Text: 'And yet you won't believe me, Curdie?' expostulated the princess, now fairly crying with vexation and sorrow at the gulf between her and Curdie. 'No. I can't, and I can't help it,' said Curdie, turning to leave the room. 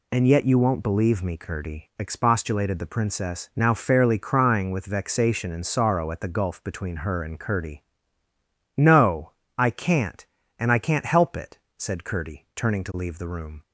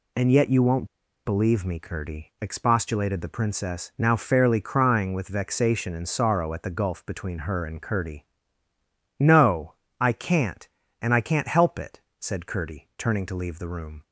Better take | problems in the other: first | pauses between "won't" and "believe"; at 0.8 s; 0.39 s long

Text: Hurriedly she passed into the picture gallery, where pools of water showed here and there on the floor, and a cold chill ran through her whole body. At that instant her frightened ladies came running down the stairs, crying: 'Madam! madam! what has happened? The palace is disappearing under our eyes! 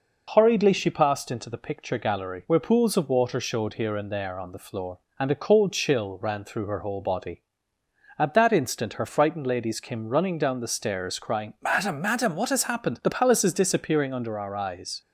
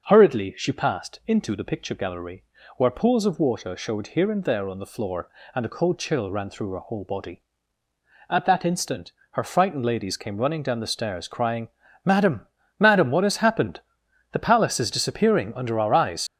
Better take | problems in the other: first | starts louder than the rest; until 1.1 s; 6 dB // pauses between "instant" and "her"; slight; at 9.1 s; 0.18 s long // leaves "eyes" unfinished; at 16.2 s; 70 ms

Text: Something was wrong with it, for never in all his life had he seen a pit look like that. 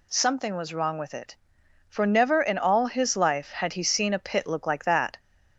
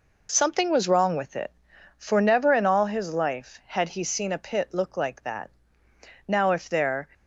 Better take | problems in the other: first | goes on to say "Now if there"; noticeable; from 6.2 s on; 0.80 s long

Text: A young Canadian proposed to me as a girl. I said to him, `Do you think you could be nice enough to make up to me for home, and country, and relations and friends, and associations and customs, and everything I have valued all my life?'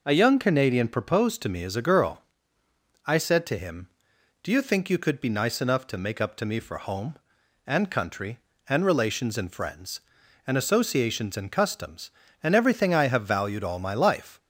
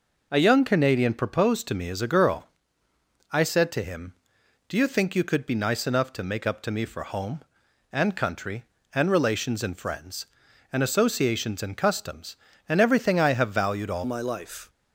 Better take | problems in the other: first | changes voice at "my"; from 14.0 s on; 0.6 s long

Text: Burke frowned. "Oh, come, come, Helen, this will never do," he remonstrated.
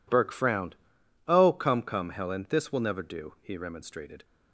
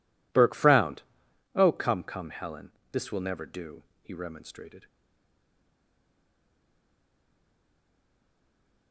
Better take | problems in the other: first | stays silent after the last word; strong; from 4.8 s on; 4.1 s long

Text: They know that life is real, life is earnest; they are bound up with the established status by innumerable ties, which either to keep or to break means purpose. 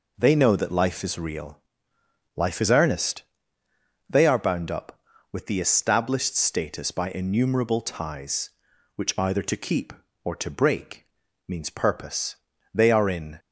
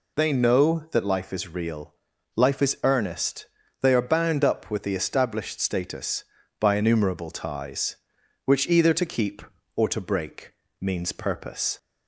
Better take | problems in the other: second | pauses between "break" and "means"; at 11.0 s; 0.40 s long; slight in the second // goes on to say "They are in"; noticeable; from 12.7 s on; 0.64 s long

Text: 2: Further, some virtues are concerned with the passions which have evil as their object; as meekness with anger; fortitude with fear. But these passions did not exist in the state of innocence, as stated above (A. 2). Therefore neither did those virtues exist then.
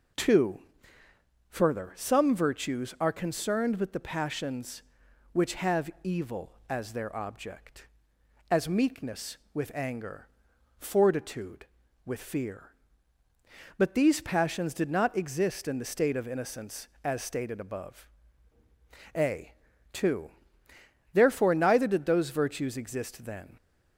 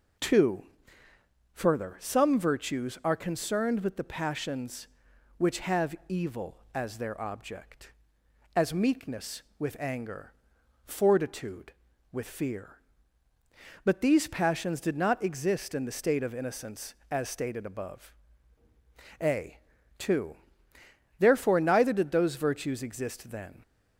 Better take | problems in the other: neither | none

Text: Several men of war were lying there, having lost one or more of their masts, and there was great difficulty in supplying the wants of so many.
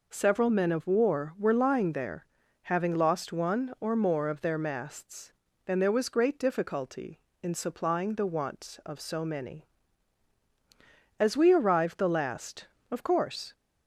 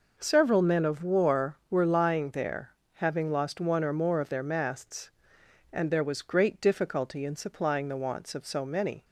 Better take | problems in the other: second | goes on to say "As we arrived the last of course"; strong; from 11.1 s on; 2.3 s long

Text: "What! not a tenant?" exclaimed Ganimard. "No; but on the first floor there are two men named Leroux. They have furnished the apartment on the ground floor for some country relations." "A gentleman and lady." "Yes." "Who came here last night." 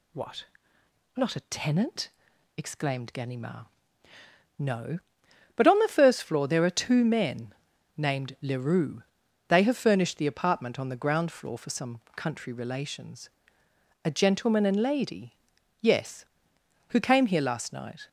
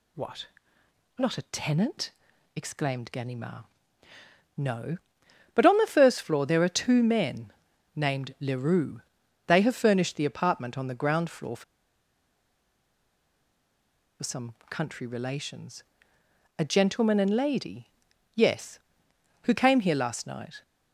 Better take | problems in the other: first | pauses between "men" and "named"; at 7.5 s; 0.44 s long; also in the first // pauses between "for" and "some"; strong; at 11.6 s; 2.5 s long // pauses between "some" and "country"; slight; at 14.5 s; 0.16 s long; slight in the first

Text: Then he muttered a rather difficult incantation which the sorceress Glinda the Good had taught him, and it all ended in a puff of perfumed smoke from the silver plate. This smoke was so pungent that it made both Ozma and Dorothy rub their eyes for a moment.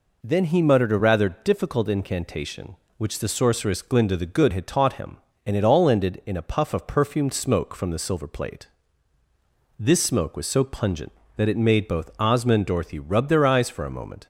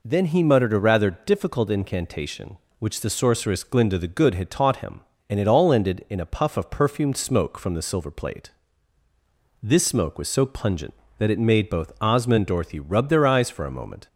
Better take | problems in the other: neither | none

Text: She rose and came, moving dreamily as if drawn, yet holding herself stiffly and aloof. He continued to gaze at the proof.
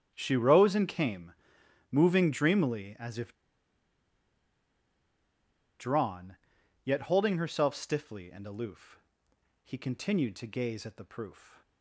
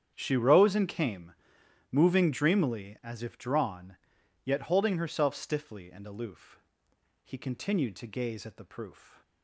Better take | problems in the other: second | starts louder than the rest; strong; until 1.1 s; 8.5 dB; strong in the second // pauses between "if" and "drawn"; strong; at 3.3 s; 2.4 s long

